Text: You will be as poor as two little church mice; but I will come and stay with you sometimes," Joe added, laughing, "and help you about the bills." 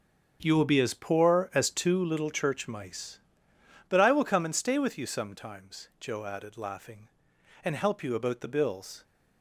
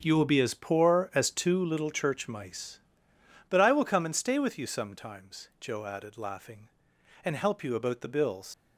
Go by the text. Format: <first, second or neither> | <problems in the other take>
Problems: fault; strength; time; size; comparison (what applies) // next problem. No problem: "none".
first | starts louder than the rest; until 1.0 s; 7 dB; strong in the first // leaves "bills" unfinished; at 8.5 s; 95 ms